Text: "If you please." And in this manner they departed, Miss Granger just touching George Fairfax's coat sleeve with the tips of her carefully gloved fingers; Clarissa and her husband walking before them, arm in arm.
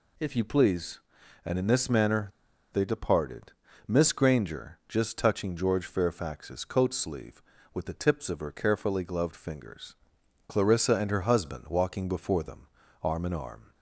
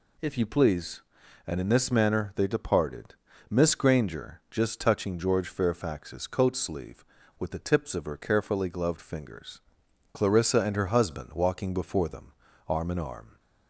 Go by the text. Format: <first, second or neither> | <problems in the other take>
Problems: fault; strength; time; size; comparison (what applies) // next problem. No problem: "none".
second | pauses between "manner" and "they"; at 2.3 s; 0.41 s long